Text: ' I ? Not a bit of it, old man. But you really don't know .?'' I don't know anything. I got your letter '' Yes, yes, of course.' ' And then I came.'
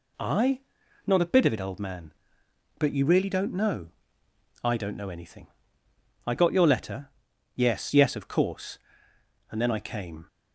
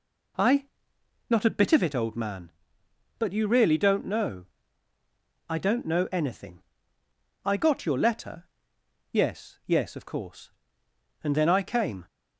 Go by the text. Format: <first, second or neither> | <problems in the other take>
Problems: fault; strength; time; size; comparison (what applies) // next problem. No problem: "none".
neither | none